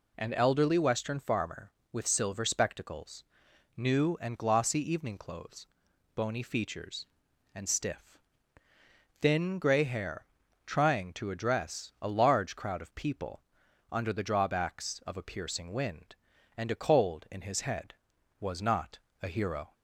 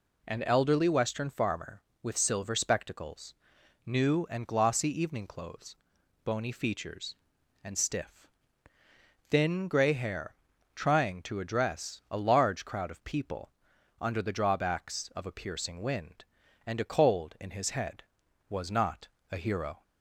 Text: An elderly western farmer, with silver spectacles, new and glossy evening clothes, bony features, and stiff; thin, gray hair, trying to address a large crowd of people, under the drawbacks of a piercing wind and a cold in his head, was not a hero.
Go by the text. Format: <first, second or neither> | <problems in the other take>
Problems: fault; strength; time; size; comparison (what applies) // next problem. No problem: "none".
neither | pauses between "not" and "a"; slight; the same in both